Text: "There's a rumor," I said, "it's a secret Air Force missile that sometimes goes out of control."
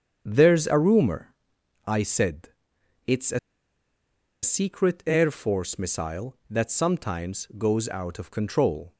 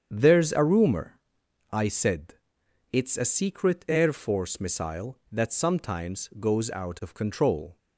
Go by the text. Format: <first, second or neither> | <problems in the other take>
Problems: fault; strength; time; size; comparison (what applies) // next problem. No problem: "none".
second | starts louder than the rest; strong; until 1.2 s; 7.5 dB; strong in the second // pauses between "a" and "secret"; at 3.3 s; 1.0 s long